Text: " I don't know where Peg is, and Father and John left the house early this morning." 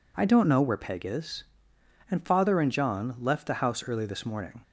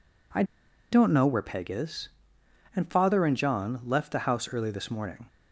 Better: first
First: none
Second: pauses between "I" and "don't"; noticeable; at 0.4 s; 0.48 s long

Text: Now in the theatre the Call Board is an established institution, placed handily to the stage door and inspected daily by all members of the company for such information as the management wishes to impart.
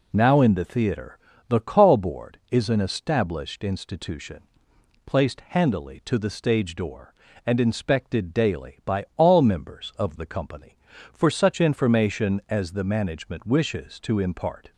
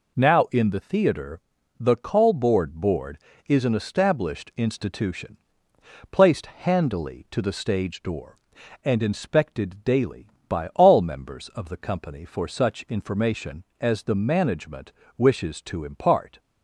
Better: first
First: pauses between "theatre" and "the"; slight; at 1.1 s; 0.30 s long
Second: pauses between "theatre" and "the"; at 1.3 s; 0.40 s long // says "Board" twice; at 2.7 s // pauses between "management" and "wishes"; slight; at 14.9 s; 0.25 s long

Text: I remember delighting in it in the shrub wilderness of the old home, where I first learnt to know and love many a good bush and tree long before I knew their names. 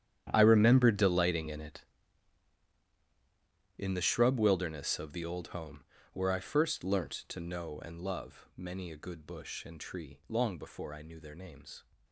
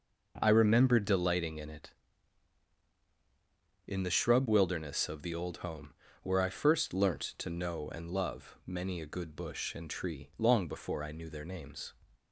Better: second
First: gets quieter; strong; throughout; 16.5 dB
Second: none

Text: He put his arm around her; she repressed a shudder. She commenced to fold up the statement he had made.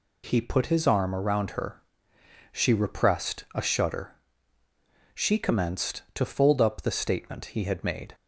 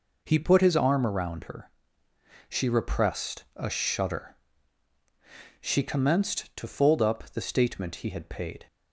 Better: first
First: none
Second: says "paid" for "made"; at 8.2 s

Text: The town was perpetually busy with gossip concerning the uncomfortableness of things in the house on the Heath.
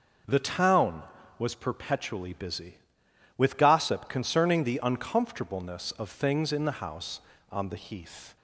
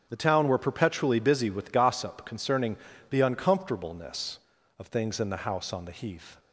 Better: first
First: starts louder than the rest; noticeable; until 1.6 s; 6 dB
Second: starts louder than the rest; until 1.1 s; 7 dB // says "were" for "was"; at 0.4 s // pauses between "concerning" and "the"; slight; at 2.7 s; 0.34 s long

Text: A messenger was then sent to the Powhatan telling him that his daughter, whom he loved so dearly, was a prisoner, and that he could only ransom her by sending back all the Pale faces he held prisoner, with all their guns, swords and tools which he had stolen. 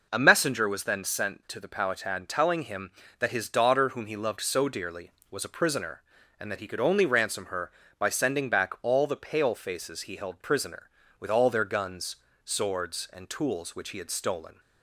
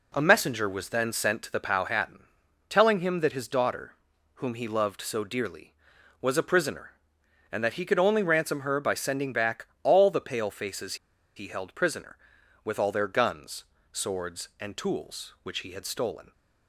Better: first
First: none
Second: pauses between "Powhatan" and "telling"; noticeable; at 2.1 s; 0.50 s long // pauses between "back" and "all"; slight; at 9.6 s; 0.16 s long // pauses between "faces" and "he"; at 10.9 s; 0.41 s long

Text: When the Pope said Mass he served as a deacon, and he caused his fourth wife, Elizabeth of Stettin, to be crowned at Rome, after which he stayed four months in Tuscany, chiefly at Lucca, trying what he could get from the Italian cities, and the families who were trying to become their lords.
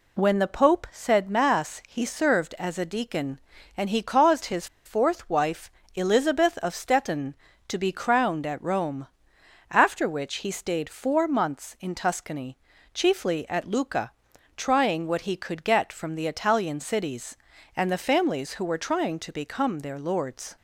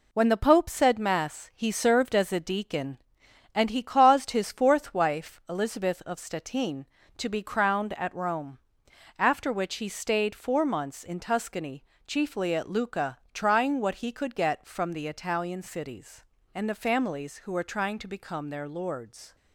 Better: second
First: pauses between "his" and "fourth"; slight; at 4.6 s; 0.19 s long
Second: none

